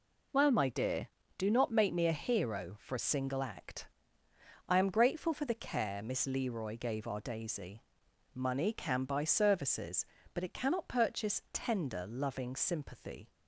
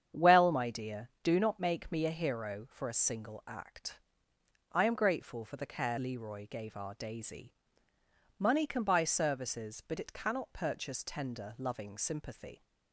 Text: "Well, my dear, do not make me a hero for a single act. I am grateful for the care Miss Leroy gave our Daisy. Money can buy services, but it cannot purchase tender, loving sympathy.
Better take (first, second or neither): first